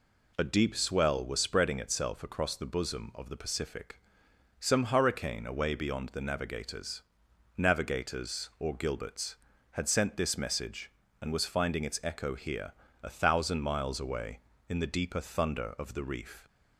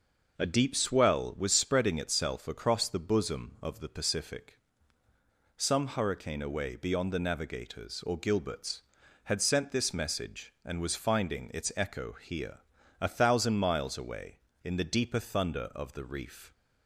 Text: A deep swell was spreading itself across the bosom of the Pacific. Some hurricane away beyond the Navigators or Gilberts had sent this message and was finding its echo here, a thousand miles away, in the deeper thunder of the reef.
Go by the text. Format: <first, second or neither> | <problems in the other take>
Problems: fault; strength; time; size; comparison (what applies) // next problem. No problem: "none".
second | says "Navigators" twice; at 7.5 s